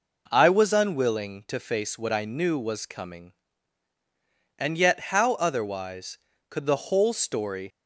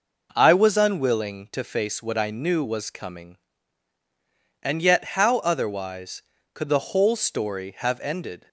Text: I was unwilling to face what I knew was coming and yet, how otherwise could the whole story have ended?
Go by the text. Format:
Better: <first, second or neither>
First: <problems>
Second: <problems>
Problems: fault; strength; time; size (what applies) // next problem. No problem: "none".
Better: second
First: stops before "have ended"; at 7.7 s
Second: none